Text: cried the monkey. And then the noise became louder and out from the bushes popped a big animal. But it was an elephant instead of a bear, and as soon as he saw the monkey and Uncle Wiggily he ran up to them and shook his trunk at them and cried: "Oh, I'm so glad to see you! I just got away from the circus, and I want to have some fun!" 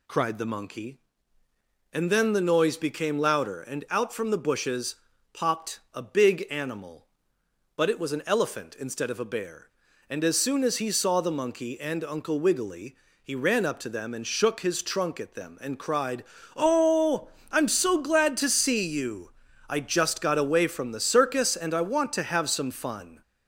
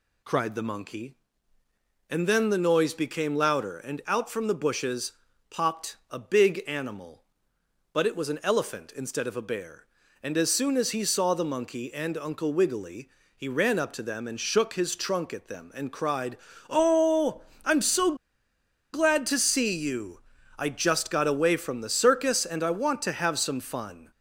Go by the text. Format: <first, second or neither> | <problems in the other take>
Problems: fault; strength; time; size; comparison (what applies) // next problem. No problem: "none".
first | pauses between "bushes" and "popped"; at 5.1 s; 0.38 s long; also in the first // pauses between "Wiggily" and "he"; slight; at 13.0 s; 0.28 s long; slight in the first // pauses between "so" and "glad"; noticeable; at 18.1 s; 0.78 s long